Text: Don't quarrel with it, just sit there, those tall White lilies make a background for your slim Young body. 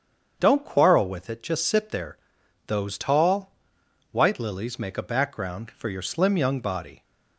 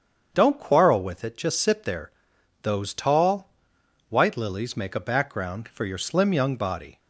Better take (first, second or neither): neither